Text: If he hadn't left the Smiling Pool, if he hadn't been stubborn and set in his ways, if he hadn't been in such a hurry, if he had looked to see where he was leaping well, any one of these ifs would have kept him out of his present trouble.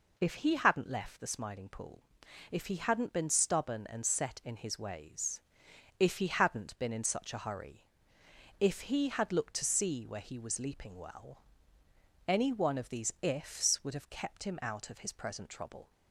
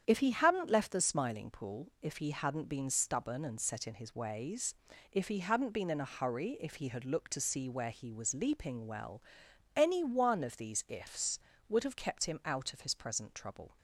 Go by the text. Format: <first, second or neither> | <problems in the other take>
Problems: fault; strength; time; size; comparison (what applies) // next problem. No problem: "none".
first | starts louder than the rest; strong; until 1.0 s; 8.5 dB // skips "such"; at 5.9 s